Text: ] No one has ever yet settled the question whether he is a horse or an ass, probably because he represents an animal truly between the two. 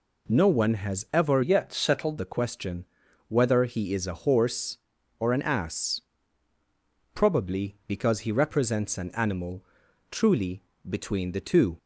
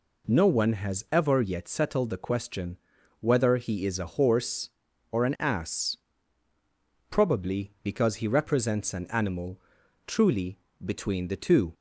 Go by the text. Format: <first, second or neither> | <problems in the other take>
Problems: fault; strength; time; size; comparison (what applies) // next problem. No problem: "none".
second | changes voice from "yet" to "settled"; from 1.4 to 2.1 s; 0.7 s long // pauses between "question" and "whether"; at 2.8 s; 0.42 s long; also in the second // pauses between "animal" and "truly"; noticeable; at 9.6 s; 0.46 s long; noticeable in the second // pauses between "truly" and "between"; slight; at 10.6 s; 0.26 s long; slight in the second